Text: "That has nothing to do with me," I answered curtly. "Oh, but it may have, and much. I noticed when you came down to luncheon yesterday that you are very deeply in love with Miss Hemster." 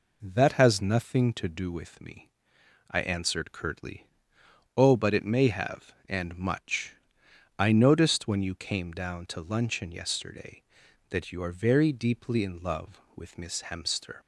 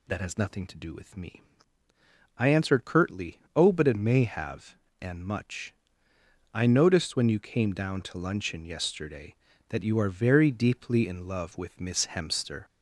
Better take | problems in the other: first | gets louder; slight; throughout; 2.5 dB

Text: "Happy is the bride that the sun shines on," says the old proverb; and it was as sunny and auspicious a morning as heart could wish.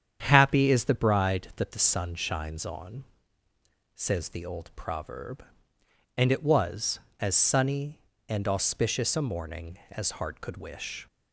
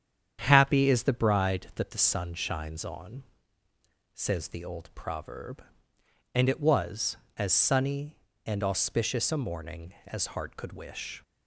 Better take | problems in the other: neither | starts louder than the rest; strong; the same in both

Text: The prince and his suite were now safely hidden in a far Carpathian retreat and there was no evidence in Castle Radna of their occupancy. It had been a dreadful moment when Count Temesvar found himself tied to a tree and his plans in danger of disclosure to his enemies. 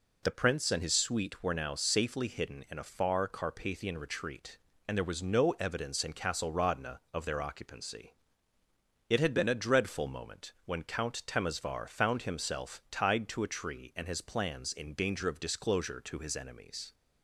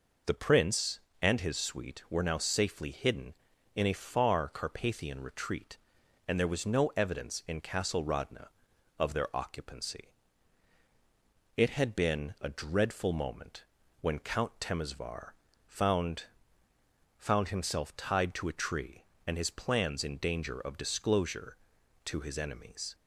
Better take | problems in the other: first | pauses between "moment" and "when"; slight; at 13.6 s; 0.36 s long // pauses between "Temesvar" and "found"; slight; at 15.3 s; 0.34 s long // says "found" twice; at 17.1 s

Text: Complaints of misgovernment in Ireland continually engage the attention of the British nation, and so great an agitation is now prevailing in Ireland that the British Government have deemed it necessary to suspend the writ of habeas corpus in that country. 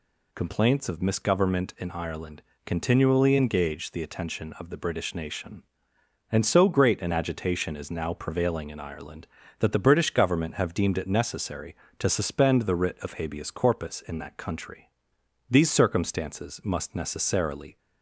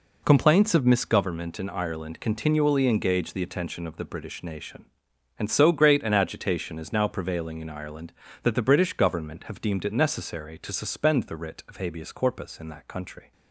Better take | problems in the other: second | pauses between "Ireland" and "continually"; slight; at 2.4 s; 0.24 s long // goes on to say "These circumstances must necessarily"; strong; from 15.5 s on; 2.2 s long

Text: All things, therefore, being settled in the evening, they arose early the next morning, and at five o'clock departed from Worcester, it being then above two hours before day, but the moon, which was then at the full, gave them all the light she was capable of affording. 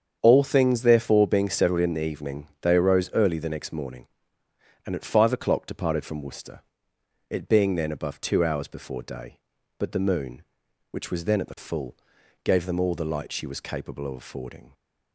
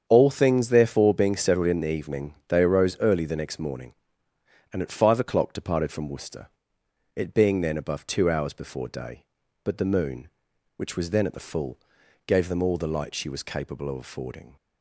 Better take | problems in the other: neither | starts louder than the rest; strong; the same in both

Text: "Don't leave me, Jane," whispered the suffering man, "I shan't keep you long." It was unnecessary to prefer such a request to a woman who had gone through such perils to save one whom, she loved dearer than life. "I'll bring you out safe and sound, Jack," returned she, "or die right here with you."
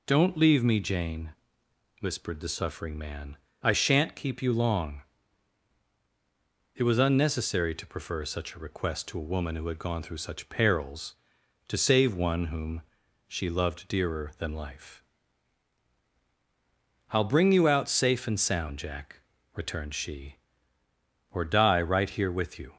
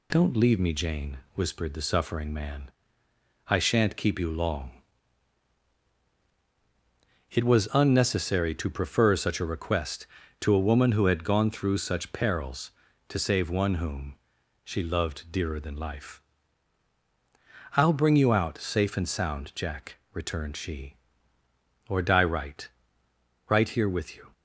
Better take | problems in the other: first | says "right" twice; at 23.4 s

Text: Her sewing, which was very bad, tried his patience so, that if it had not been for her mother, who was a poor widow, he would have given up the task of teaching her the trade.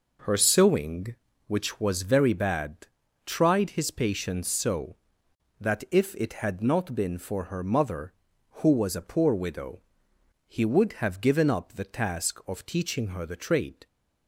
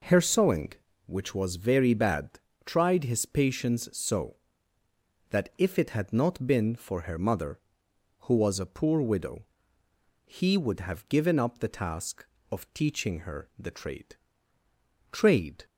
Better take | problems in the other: first | says "trade" twice; at 15.1 s

